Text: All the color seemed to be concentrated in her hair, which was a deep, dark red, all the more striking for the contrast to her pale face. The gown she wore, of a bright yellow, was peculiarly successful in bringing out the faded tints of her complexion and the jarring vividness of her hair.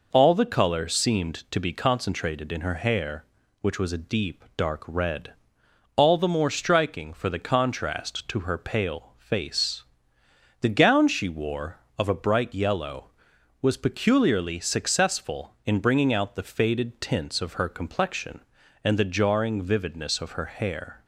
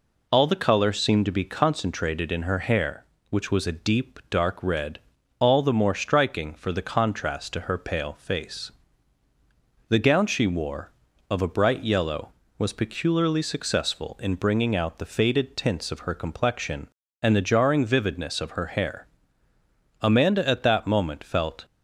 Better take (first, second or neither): first